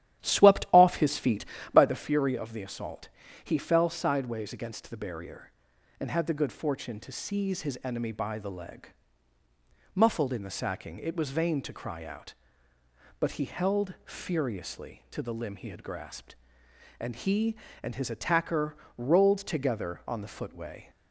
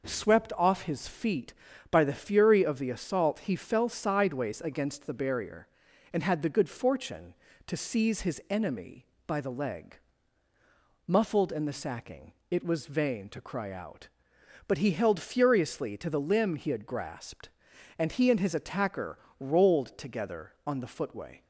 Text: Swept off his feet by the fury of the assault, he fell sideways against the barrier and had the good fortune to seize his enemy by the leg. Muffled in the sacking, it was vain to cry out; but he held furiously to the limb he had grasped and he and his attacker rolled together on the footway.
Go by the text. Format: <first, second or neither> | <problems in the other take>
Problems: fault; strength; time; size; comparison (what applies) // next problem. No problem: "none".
second | starts louder than the rest; strong; until 1.8 s; 12 dB // pauses between "attacker" and "rolled"; slight; at 18.7 s; 0.22 s long; slight in the second